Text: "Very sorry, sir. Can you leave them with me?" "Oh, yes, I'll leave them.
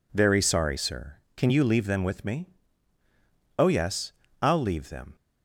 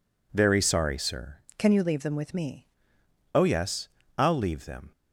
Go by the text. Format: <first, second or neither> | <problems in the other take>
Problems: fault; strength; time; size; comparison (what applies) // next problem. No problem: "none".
first | changes voice from "Can" to "me"; from 1.5 to 2.6 s; 1.1 s long